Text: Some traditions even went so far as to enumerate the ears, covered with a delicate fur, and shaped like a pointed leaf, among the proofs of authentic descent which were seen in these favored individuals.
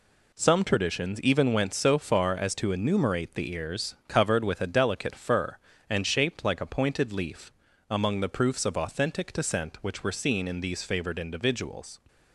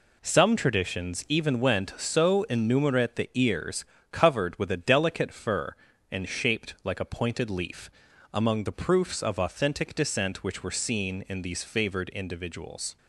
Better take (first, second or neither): first